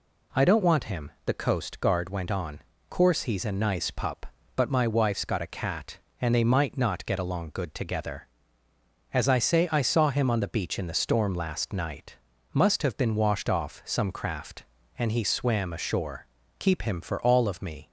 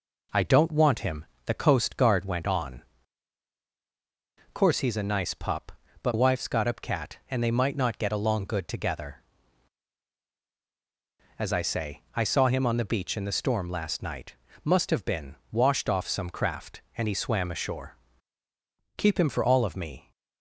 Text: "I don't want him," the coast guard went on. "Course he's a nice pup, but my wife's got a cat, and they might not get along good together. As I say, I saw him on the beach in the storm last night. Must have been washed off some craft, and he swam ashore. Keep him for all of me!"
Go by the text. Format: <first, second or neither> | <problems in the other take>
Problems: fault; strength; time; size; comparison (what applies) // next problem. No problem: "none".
first | skips "my"; at 6.1 s // pauses between "been" and "washed"; slight; at 15.3 s; 0.16 s long